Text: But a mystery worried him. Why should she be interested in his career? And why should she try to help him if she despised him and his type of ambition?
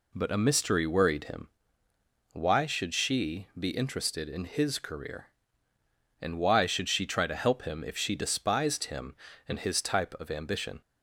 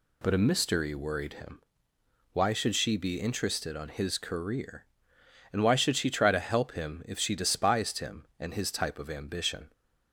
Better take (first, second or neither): first